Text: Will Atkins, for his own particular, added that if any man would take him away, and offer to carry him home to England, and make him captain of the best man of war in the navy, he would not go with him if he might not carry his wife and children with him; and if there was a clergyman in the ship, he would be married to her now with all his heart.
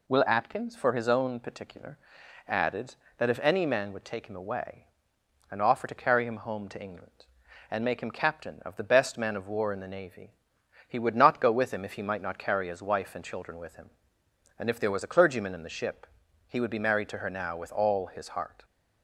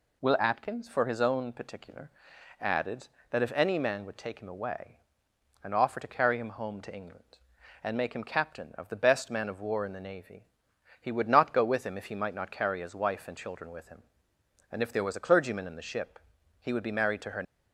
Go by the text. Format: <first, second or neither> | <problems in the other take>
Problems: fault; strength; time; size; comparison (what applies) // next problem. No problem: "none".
first | stops before "now with all his heart"; at 17.4 s